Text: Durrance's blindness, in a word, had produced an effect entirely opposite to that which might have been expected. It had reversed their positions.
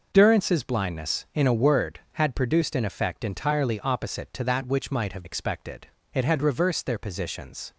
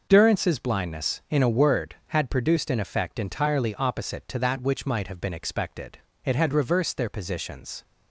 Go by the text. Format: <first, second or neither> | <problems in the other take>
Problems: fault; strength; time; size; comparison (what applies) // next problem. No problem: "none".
second | skips "been"; at 5.2 s